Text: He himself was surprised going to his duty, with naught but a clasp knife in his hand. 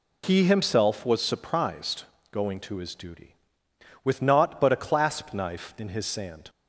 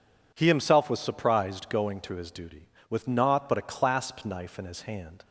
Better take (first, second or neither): second